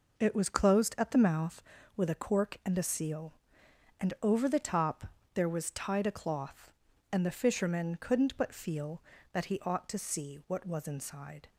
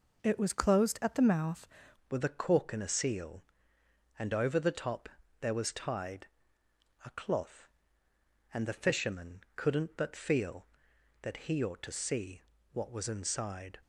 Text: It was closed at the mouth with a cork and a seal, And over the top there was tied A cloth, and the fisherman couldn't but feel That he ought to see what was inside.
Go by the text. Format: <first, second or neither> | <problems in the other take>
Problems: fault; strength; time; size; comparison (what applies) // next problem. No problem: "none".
first | changes voice at "with"; from 2.1 s on; 11.6 s long // pauses between "top" and "there"; slight; at 5.0 s; 0.30 s long; slight in the first // pauses between "tied" and "A"; noticeable; at 6.2 s; 0.78 s long // pauses between "see" and "what"; slight; at 12.4 s; 0.30 s long